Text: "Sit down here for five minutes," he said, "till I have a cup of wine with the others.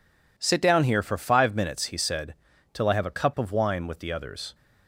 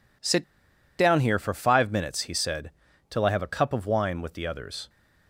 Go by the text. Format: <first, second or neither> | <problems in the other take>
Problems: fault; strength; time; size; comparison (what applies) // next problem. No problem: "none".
first | pauses between "Sit" and "down"; noticeable; at 0.4 s; 0.56 s long